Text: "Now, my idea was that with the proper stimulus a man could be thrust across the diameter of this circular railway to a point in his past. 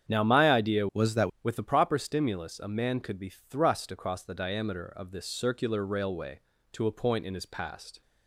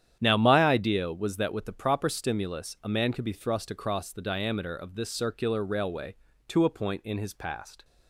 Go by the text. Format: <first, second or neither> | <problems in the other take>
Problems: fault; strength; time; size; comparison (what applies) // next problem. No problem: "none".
second | starts louder than the rest; strong; until 1.1 s; 8.5 dB; strong in the second // changes voice from "was" to "that"; from 0.9 to 1.2 s; 0.3 s long